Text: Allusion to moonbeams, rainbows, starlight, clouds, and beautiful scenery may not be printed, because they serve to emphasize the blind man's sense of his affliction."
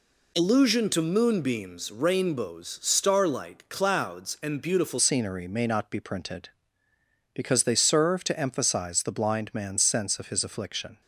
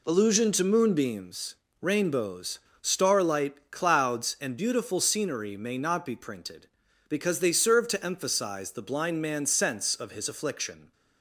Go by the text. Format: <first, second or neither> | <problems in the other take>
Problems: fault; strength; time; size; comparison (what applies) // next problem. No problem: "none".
second | changes voice at "scenery"; from 4.9 s on; 6.1 s long